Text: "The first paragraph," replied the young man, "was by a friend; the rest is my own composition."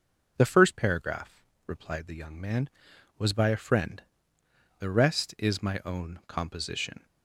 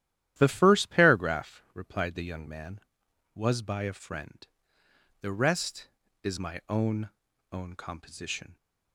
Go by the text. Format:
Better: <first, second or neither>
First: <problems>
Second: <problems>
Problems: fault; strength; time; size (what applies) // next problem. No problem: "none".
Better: first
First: none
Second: starts louder than the rest; strong; until 1.3 s; 12 dB // says "own" twice; at 7.5 s